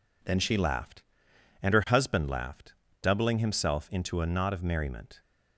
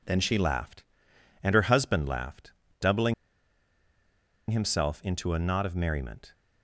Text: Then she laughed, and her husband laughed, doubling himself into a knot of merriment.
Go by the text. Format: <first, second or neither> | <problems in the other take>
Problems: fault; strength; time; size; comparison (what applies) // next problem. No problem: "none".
first | pauses between "doubling" and "himself"; strong; at 3.1 s; 1.3 s long